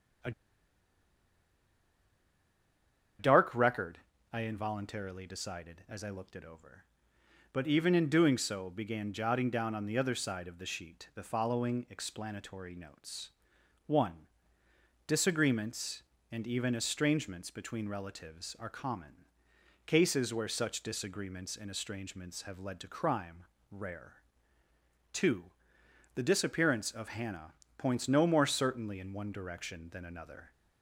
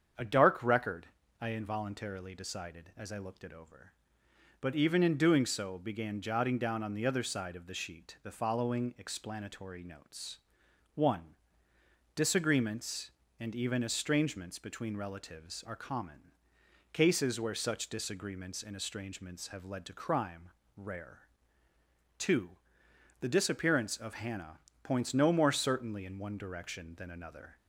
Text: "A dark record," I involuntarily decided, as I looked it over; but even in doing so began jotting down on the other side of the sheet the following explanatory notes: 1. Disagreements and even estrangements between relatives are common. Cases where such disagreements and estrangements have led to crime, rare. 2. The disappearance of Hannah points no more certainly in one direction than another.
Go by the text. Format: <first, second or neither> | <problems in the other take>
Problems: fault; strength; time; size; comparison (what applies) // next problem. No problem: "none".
second | starts louder than the rest; strong; until 4.4 s; 7.5 dB; strong in the second // pauses between "A" and "dark"; strong; at 0.3 s; 2.8 s long // pauses between "Hannah" and "points"; slight; at 27.5 s; 0.24 s long; slight in the second